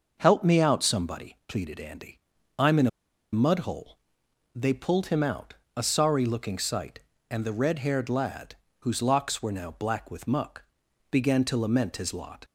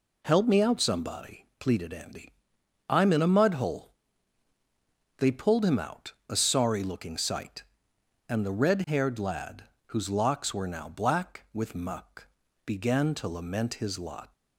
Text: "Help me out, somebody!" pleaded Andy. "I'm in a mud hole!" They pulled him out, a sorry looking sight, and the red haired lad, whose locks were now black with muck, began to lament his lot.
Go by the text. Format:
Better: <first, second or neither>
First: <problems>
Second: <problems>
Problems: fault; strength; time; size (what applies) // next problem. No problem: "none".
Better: second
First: starts louder than the rest; noticeable; until 1.2 s; 6 dB // pauses between "in" and "a"; at 2.8 s; 0.44 s long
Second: none